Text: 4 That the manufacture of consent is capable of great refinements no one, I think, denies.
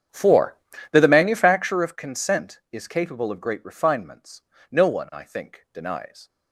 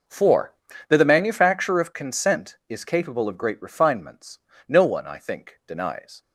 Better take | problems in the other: second | starts louder than the rest; strong; until 1.8 s; 8.5 dB // pauses between "refinements" and "no"; slight; at 4.4 s; 0.30 s long; slight in the second

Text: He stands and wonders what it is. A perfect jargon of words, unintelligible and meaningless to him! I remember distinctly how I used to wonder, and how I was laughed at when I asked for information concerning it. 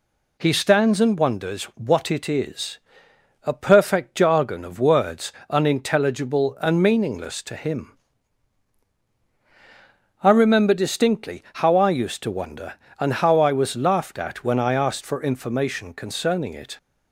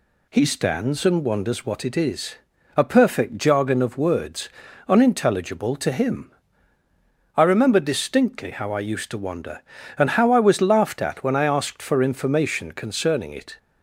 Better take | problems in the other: first | skips "and meaningless"; at 5.7 s

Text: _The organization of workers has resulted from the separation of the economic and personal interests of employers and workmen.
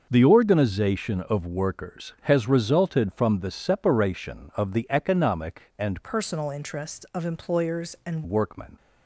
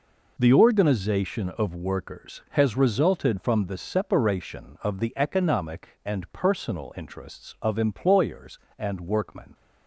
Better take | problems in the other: second | starts louder than the rest; noticeable; until 1.1 s; 6 dB // changes voice from "personal" to "and"; from 6.0 to 8.2 s; 2.2 s long

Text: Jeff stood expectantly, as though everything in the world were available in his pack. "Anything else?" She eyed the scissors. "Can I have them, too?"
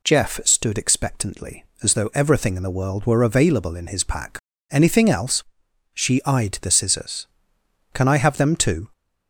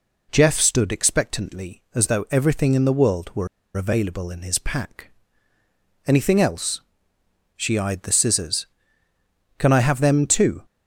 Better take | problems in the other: first | pauses between "were" and "available"; slight; at 3.4 s; 0.28 s long

